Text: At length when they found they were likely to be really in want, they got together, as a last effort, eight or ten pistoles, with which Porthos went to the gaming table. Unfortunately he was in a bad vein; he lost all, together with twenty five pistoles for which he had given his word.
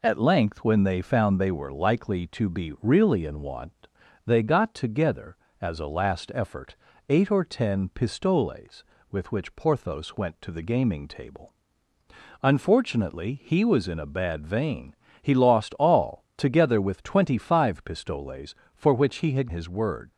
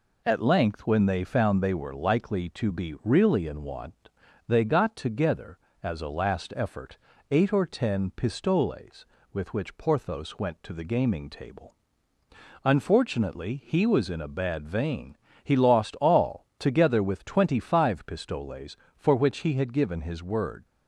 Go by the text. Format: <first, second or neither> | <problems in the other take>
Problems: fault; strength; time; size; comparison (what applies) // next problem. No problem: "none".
second | skips "given"; at 19.4 s